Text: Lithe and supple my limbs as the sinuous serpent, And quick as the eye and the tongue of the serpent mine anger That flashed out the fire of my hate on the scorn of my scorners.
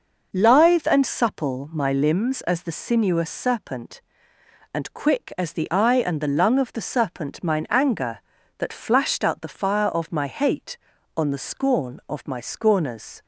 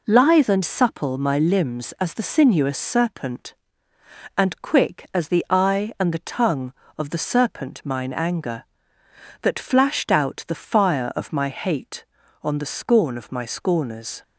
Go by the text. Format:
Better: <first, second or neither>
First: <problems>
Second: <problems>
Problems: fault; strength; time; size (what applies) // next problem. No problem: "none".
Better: second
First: says "lung" for "tongue"; at 6.2 s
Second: none